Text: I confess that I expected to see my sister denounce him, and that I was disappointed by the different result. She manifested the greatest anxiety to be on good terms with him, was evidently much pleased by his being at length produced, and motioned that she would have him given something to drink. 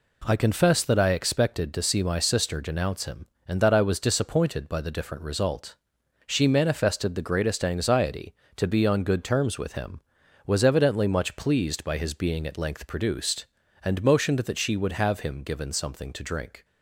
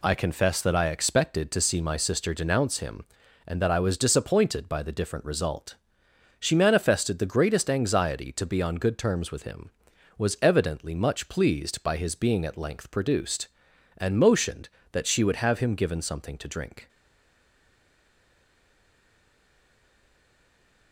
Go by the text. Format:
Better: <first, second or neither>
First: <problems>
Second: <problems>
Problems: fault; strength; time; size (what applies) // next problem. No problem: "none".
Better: first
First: none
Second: stays silent after the last word; strong; from 16.8 s on; 4.1 s long